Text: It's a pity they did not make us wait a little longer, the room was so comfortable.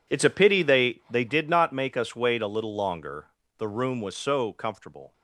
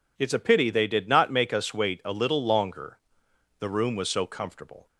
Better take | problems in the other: second | says "they" twice; at 1.1 s

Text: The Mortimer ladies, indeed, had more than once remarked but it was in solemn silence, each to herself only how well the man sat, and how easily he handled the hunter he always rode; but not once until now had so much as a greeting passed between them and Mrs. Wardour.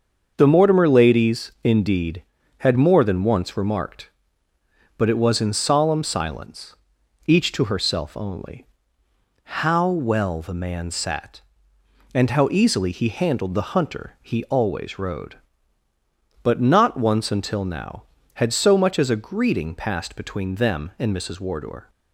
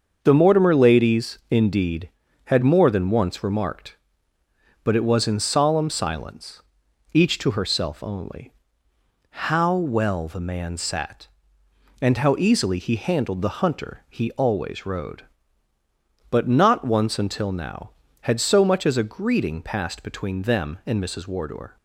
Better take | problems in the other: neither | starts louder than the rest; the same in both // pauses between "only" and "how"; noticeable; the same in both

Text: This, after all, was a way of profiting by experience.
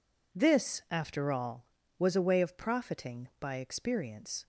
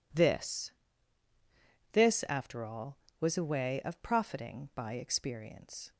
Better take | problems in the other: first | says "This" twice; at 1.9 s

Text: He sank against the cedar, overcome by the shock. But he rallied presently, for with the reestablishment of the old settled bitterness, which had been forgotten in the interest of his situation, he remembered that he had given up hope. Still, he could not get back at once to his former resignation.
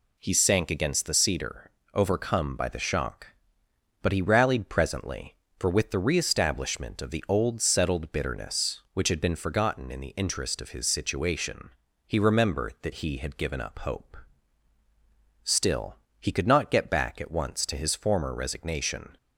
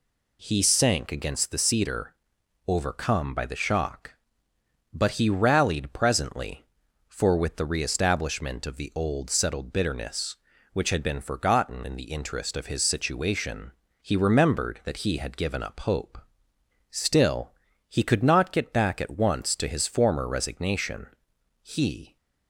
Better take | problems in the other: first | goes on to say "He"; from 21.6 s on; 0.56 s long

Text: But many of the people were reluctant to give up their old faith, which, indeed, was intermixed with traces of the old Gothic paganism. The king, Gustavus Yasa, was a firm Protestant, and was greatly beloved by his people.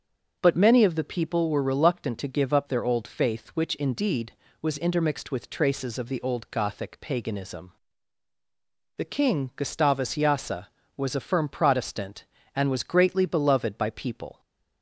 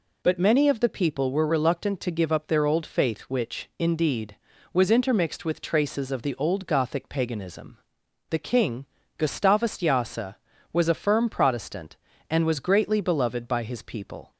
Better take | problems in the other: second | starts louder than the rest; noticeable; until 1.4 s; 6 dB // skips "his"; at 13.8 s

